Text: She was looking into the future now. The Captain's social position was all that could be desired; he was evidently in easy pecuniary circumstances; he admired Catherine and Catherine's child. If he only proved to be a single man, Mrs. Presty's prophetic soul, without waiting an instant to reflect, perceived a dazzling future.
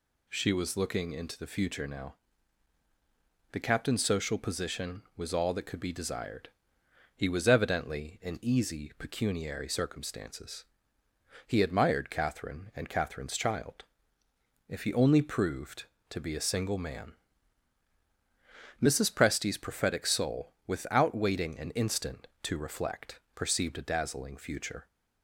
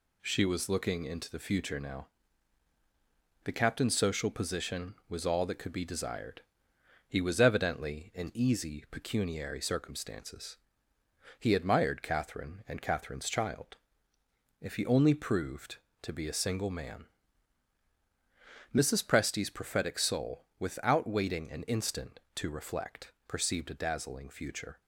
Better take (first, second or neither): first